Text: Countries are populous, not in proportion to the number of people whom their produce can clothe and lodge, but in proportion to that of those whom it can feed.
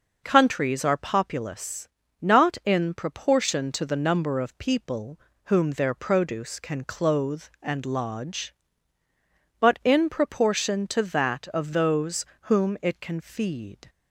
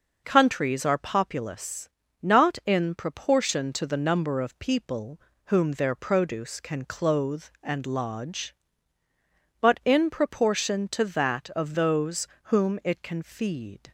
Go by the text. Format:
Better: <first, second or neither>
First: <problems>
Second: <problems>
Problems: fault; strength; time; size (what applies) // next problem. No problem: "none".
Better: neither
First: pauses between "people" and "whom"; slight; at 5.2 s; 0.26 s long // pauses between "those" and "whom"; slight; at 12.2 s; 0.20 s long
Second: pauses between "people" and "whom"; slight; at 5.2 s; 0.26 s long // pauses between "those" and "whom"; slight; at 12.2 s; 0.20 s long